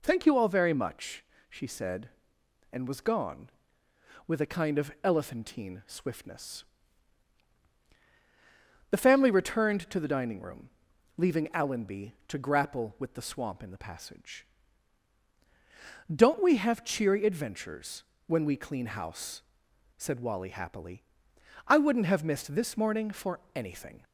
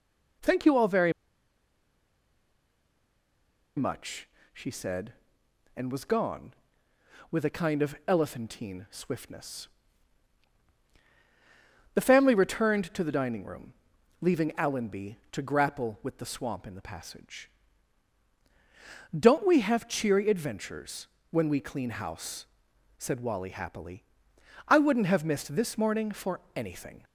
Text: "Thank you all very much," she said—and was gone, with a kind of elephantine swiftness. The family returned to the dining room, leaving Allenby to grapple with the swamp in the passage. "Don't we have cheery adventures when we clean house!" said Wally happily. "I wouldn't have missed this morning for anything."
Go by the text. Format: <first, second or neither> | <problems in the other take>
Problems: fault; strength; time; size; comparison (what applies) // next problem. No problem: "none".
first | pauses between "very" and "much"; strong; at 1.1 s; 2.6 s long // pauses between "adventures" and "when"; slight; at 21.0 s; 0.24 s long; slight in the first // pauses between "for" and "anything"; slight; at 26.3 s; 0.16 s long; slight in the first